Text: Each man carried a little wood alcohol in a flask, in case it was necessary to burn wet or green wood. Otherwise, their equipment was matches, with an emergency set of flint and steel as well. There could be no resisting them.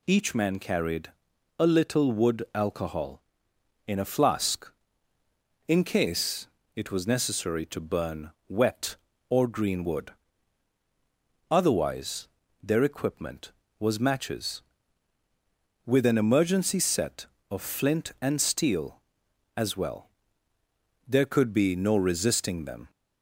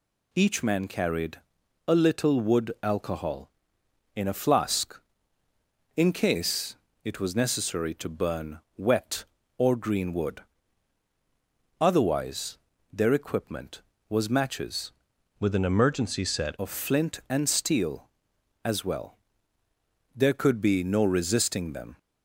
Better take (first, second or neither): first